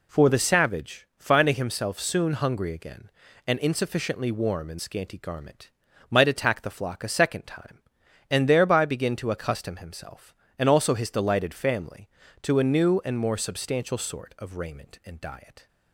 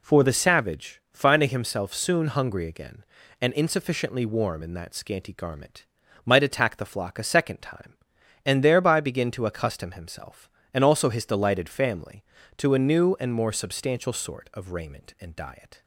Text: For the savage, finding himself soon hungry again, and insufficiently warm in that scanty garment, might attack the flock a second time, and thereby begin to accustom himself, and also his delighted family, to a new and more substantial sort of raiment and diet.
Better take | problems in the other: second | skips "that"; at 4.8 s

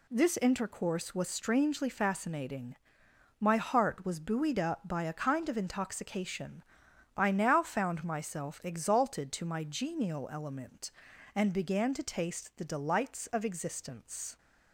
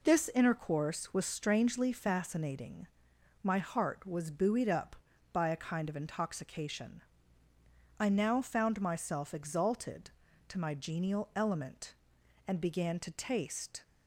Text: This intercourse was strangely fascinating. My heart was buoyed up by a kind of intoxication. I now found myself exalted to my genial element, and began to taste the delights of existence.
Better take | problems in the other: first | stops before "the delights of existence"; at 13.8 s

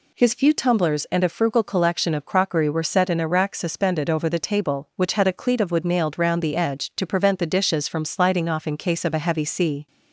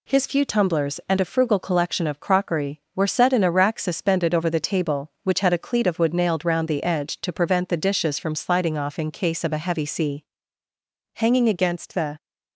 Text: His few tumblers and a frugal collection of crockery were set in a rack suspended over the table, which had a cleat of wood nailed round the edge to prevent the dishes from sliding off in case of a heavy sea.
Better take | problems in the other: first | goes on to say "Hanging against the"; noticeable; from 11.1 s on; 1.0 s long

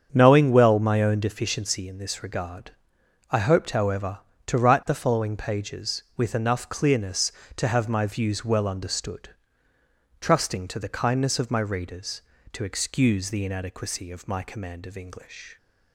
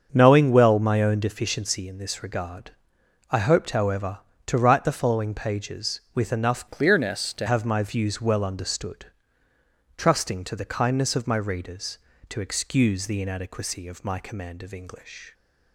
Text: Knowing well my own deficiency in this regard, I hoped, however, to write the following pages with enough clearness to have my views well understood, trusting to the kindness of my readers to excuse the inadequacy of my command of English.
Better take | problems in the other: first | starts louder than the rest; until 1.1 s; 6.5 dB; also in the first // changes voice from "clearness" to "to"; from 6.7 to 7.4 s; 0.7 s long

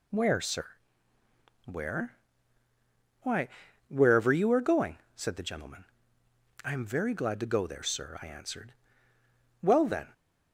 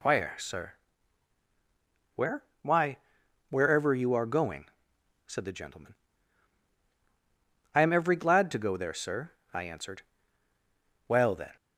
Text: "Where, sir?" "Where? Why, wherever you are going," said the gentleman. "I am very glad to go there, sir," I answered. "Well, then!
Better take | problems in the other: first | says "every" for "very"; at 7.9 s

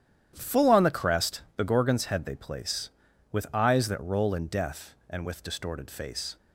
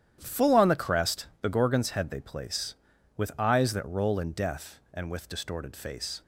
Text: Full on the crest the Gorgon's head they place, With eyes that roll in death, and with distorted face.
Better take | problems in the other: neither | starts louder than the rest; strong; the same in both

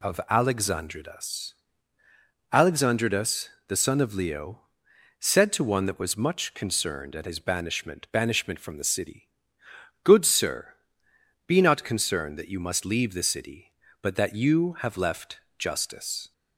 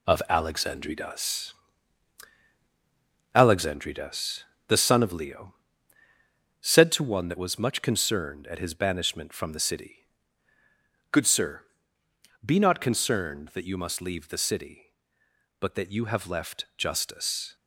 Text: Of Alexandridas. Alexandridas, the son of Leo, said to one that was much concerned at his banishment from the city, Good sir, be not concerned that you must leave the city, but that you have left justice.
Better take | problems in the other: second | says "banishment" twice; at 8.0 s // pauses between "left" and "justice"; slight; at 15.3 s; 0.18 s long

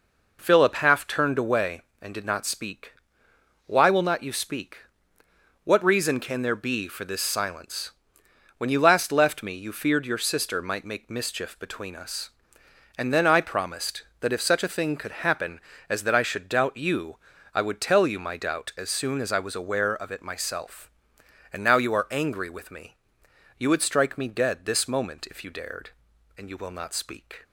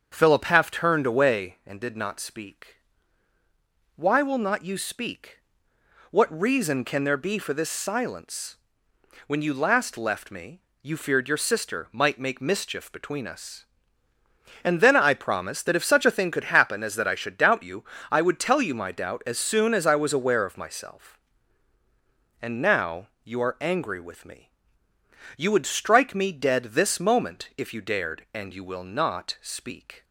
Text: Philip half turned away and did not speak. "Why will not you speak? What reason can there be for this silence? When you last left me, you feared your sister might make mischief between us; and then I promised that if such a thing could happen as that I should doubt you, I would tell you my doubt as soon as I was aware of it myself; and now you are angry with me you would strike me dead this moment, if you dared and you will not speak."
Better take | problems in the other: first | starts louder than the rest; until 1.1 s; 7 dB // skips "it"; at 20.5 s // pauses between "now" and "you"; slight; at 23.0 s; 0.18 s long // pauses between "me" and "you"; noticeable; at 24.4 s; 0.88 s long; noticeable in the first

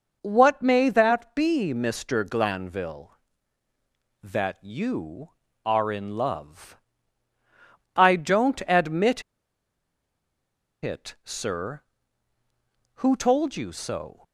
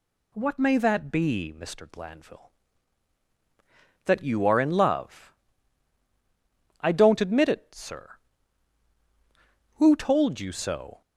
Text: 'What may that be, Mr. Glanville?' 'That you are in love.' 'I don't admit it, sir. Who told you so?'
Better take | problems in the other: second | pauses between "admit" and "it"; strong; at 9.2 s; 1.6 s long

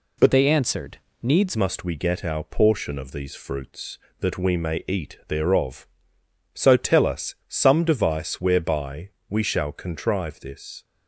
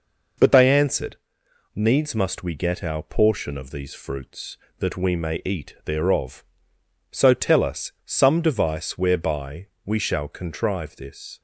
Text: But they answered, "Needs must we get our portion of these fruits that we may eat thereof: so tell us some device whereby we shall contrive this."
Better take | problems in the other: second | changes voice from "they" to "Needs"; from 0.3 to 1.5 s; 1.2 s long // pauses between "whereby" and "we"; slight; at 9.1 s; 0.18 s long; slight in the second

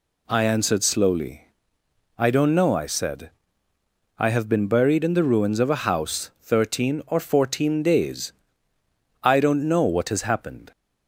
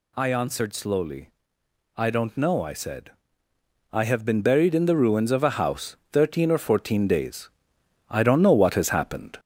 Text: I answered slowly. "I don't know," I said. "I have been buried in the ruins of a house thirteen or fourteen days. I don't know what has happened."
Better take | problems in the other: first | gets louder; slight; throughout; 2.5 dB // pauses between "house" and "thirteen"; slight; at 5.9 s; 0.16 s long

